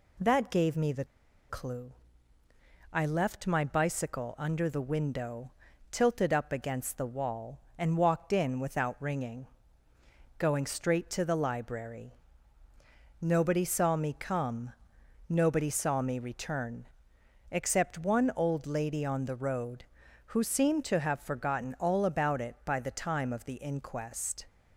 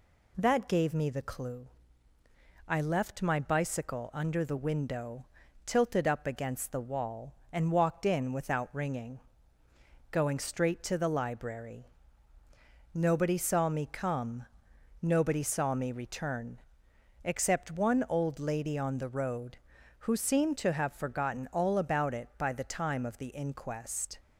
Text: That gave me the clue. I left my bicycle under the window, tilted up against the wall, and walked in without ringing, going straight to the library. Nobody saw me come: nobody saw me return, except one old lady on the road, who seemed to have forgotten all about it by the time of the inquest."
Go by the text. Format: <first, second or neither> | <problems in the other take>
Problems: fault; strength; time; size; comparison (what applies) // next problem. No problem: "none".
second | pauses between "the" and "clue"; at 1.0 s; 0.45 s long